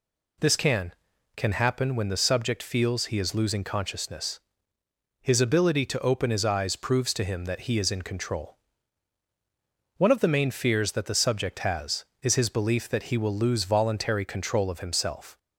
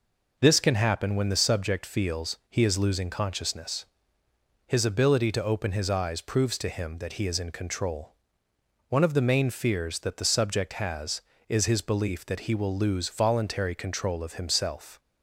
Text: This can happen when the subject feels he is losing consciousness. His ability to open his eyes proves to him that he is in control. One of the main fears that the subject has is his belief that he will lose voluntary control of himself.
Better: second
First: says "can" twice; at 1.3 s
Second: none

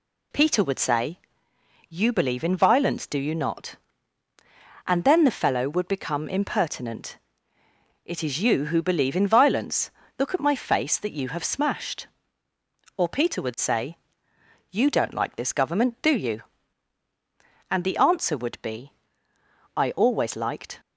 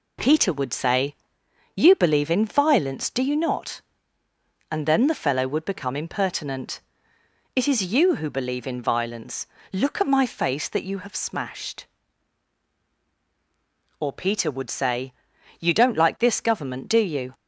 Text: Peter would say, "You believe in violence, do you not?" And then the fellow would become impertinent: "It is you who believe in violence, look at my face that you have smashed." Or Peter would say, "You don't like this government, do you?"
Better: second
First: goes on to say "And the answer would be I always liked"; strong; from 17.6 s on; 3.1 s long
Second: none

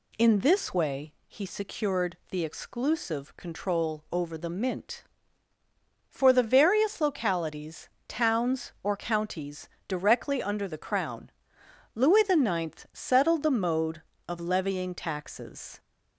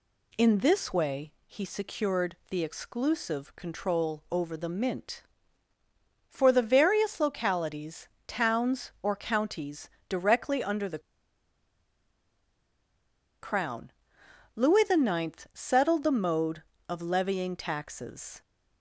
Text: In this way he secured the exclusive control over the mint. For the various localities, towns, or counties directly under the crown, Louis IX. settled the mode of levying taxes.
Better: first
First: pauses between "counties" and "directly"; slight; at 9.6 s; 0.18 s long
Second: pauses between "counties" and "directly"; slight; at 9.9 s; 0.18 s long // pauses between "the" and "crown"; strong; at 10.9 s; 2.4 s long

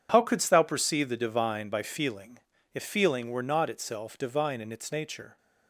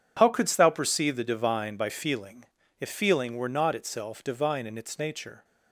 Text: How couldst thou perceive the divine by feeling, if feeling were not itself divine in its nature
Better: neither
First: none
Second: none

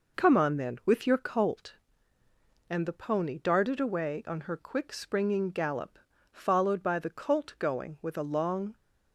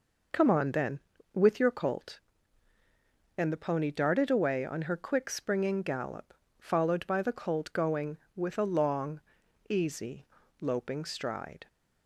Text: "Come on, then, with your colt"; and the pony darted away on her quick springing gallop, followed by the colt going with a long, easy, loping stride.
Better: second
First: stops before "easy loping stride"; at 8.7 s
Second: none

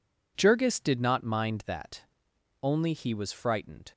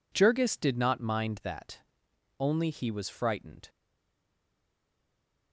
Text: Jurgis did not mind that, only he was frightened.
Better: first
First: none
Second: stays silent after the last word; noticeable; from 3.6 s on; 1.9 s long

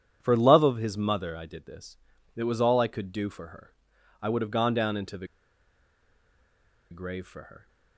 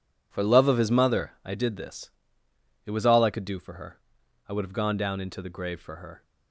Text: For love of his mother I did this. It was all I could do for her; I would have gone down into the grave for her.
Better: second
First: pauses between "the" and "grave"; strong; at 5.2 s; 1.6 s long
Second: none

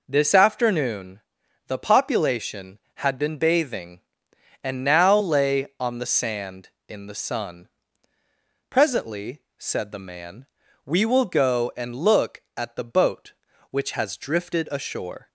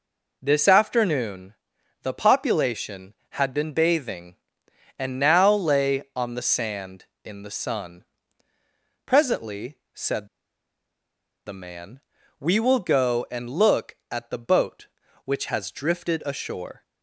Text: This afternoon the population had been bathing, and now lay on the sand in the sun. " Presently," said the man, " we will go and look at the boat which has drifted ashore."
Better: first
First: pauses between "afternoon" and "the"; noticeable; at 1.1 s; 0.48 s long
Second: pauses between "afternoon" and "the"; noticeable; at 1.5 s; 0.50 s long // pauses between "said" and "the"; at 10.2 s; 1.1 s long

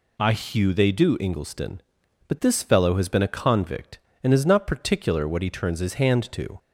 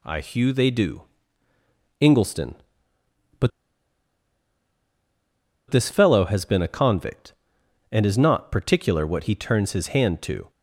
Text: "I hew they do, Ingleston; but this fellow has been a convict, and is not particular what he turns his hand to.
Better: first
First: none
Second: pauses between "but" and "this"; strong; at 3.5 s; 2.1 s long

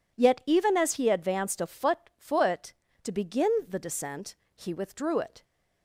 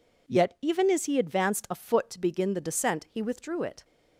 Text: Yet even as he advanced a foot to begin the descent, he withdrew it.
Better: second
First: says "foot" twice; at 2.1 s // pauses between "begin" and "the"; slight; at 3.5 s; 0.16 s long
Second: none

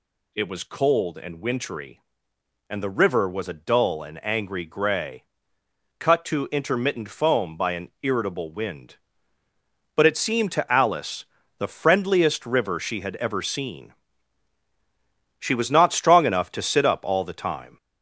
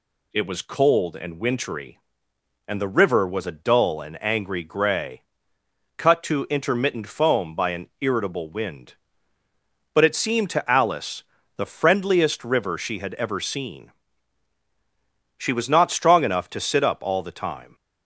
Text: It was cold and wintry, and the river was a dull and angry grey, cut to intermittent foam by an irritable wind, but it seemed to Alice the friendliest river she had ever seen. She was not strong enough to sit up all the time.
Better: second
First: gets louder; noticeable; throughout; 5 dB // pauses between "Alice" and "the"; slight; at 11.2 s; 0.34 s long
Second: pauses between "Alice" and "the"; slight; at 11.2 s; 0.34 s long

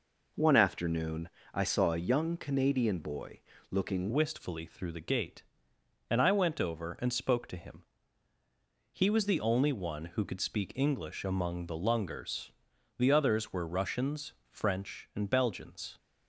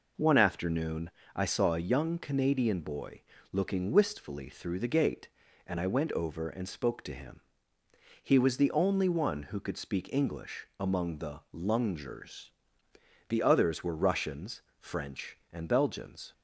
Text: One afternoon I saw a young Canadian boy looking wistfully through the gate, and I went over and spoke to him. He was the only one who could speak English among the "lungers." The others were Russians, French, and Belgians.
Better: second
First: pauses between "afternoon" and "I"; slight; at 1.2 s; 0.24 s long // pauses between "boy" and "looking"; slight; at 3.4 s; 0.28 s long // changes voice at "wistfully"; from 4.1 s on; 11.8 s long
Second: pauses between "afternoon" and "I"; slight; at 1.1 s; 0.24 s long // pauses between "boy" and "looking"; slight; at 3.2 s; 0.28 s long

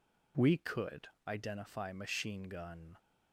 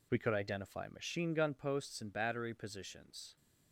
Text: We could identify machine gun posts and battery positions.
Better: second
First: pauses between "could" and "identify"; slight; at 1.0 s; 0.18 s long // stops before "posts and battery positions"; at 2.9 s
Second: none

